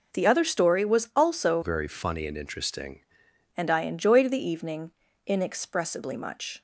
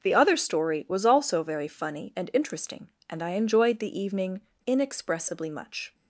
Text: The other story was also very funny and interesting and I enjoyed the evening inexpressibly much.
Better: second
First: changes voice from "very" to "interesting"; from 1.6 to 2.9 s; 1.3 s long // pauses between "evening" and "inexpressibly"; slight; at 4.9 s; 0.34 s long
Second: pauses between "evening" and "inexpressibly"; slight; at 4.4 s; 0.25 s long

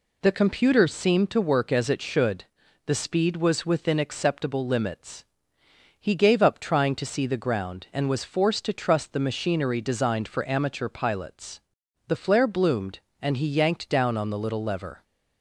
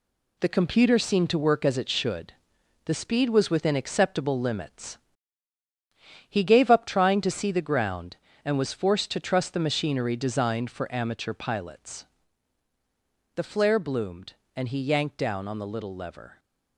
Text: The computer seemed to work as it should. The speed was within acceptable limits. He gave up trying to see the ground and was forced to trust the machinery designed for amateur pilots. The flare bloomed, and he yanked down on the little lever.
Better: first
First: none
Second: gets quieter; throughout; 7 dB

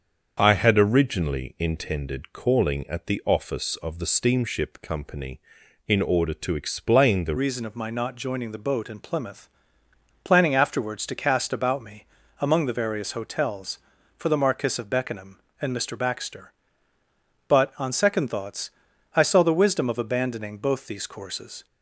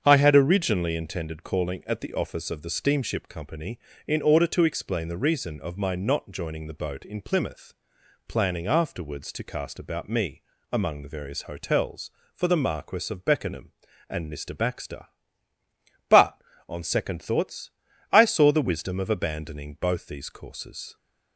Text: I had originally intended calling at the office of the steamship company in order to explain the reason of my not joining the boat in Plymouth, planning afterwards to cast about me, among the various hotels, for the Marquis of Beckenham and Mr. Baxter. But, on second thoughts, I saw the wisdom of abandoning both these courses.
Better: second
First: starts louder than the rest; until 1.4 s; 6.5 dB // changes voice at "reason"; from 7.3 s on; 14.3 s long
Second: starts louder than the rest; strong; until 1.0 s; 7.5 dB

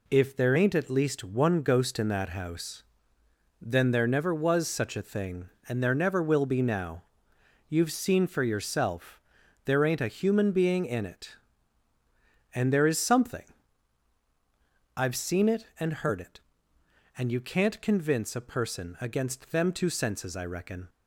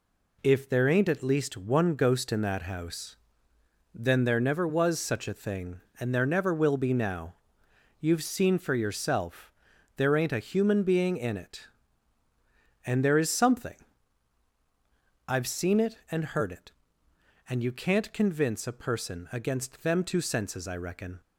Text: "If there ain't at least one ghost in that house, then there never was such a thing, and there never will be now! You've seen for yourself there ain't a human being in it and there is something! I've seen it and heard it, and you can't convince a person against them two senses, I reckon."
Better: neither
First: pauses between "yourself" and "there"; noticeable; at 9.1 s; 0.46 s long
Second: pauses between "yourself" and "there"; noticeable; at 9.5 s; 0.46 s long

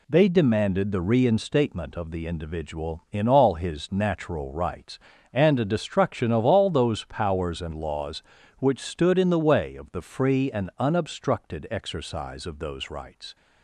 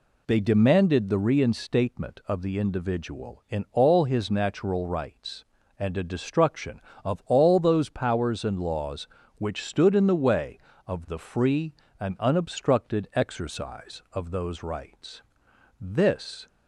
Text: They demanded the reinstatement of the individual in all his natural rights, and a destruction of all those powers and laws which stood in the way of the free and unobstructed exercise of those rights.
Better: first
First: none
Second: goes on to say "This"; noticeable; from 15.8 s on; 0.66 s long

